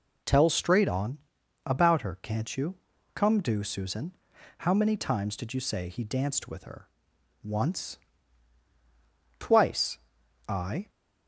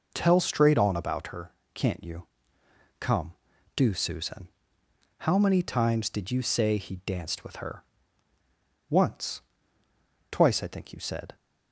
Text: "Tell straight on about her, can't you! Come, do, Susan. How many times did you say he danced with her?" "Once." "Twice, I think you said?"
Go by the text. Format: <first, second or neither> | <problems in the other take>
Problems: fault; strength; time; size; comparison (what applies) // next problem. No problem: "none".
second | pauses between "on" and "about"; noticeable; at 1.1 s; 0.46 s long // stops before "think you said"; at 10.8 s